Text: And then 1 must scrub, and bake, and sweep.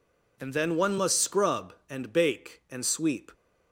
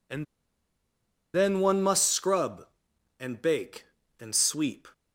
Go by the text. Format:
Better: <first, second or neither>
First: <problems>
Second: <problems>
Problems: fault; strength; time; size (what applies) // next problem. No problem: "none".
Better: first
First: none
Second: pauses between "And" and "then"; at 0.2 s; 1.0 s long